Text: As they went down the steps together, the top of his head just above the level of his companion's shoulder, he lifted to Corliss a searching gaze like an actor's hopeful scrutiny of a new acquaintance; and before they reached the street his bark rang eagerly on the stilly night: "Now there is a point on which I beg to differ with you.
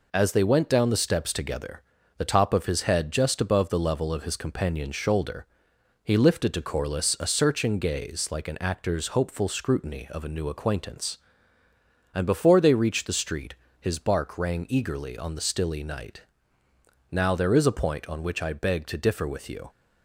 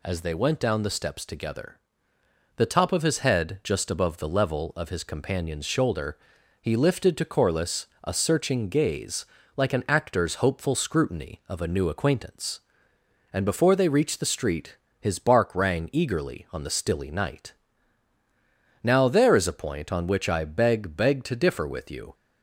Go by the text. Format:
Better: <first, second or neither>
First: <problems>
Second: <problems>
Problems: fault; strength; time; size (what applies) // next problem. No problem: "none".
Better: first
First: pauses between "street" and "his"; slight; at 13.5 s; 0.26 s long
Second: pauses between "Corliss" and "a"; slight; at 7.8 s; 0.18 s long // pauses between "gaze" and "like"; slight; at 9.2 s; 0.30 s long // pauses between "street" and "his"; slight; at 14.7 s; 0.24 s long // says "beg" twice; at 20.9 s